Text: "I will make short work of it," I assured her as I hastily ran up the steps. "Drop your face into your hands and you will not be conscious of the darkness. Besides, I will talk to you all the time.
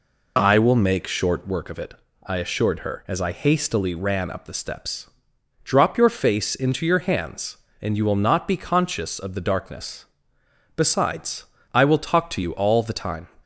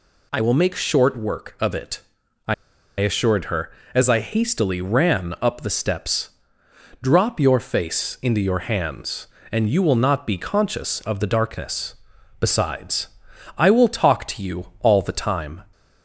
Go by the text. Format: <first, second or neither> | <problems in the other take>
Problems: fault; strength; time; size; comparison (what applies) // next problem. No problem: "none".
first | pauses between "I" and "assured"; noticeable; at 2.5 s; 0.46 s long